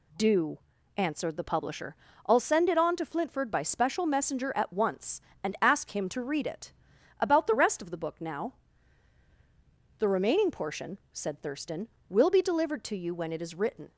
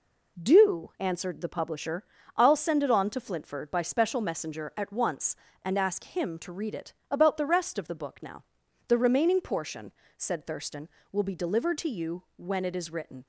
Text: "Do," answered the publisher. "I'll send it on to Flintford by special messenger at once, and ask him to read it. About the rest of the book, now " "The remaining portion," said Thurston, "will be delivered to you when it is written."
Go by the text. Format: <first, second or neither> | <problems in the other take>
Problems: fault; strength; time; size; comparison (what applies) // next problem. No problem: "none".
neither | none